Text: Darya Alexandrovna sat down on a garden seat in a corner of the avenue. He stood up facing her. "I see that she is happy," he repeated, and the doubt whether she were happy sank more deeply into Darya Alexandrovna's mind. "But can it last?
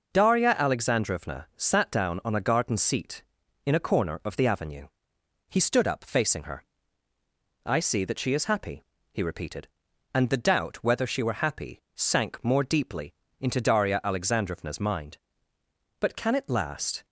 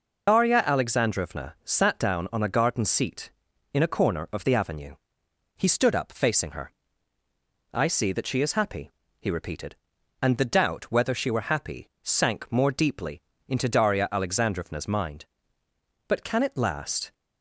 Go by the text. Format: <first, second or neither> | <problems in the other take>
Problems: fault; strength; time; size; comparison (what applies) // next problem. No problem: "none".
first | loses the start of "Darya"; at 0.2 s; 60 ms // pauses between "deeply" and "into"; slight; at 13.2 s; 0.26 s long; slight in the first